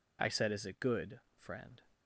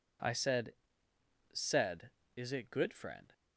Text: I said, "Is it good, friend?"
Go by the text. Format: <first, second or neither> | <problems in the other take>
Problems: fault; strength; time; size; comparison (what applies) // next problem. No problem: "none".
first | says "said" twice; at 1.5 s